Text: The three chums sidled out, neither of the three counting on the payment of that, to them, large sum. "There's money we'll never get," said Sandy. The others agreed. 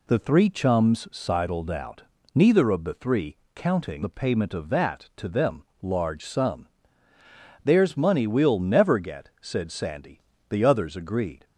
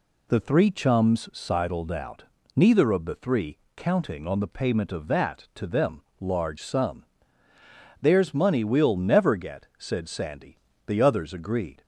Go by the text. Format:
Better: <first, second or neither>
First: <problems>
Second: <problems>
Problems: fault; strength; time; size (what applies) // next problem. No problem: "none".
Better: second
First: pauses between "three" and "counting"; slight; at 3.3 s; 0.18 s long // skips "on"; at 4.0 s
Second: pauses between "three" and "counting"; slight; at 3.5 s; 0.18 s long